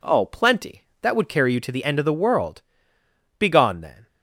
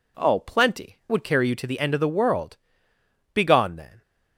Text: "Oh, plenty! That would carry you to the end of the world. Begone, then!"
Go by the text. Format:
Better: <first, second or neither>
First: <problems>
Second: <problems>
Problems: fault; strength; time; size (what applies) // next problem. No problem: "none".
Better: first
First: none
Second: skips "That"; at 1.0 s